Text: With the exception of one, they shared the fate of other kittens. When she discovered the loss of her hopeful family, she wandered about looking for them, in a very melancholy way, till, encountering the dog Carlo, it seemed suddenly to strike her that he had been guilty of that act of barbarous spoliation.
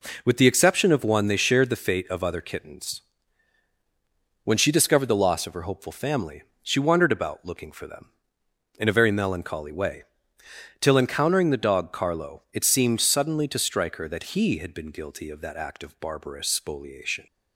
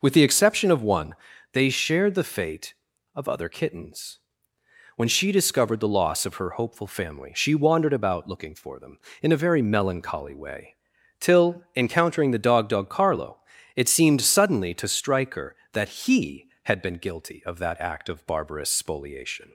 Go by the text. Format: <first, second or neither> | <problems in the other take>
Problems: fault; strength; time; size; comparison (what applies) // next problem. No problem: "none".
first | says "dog" twice; at 12.6 s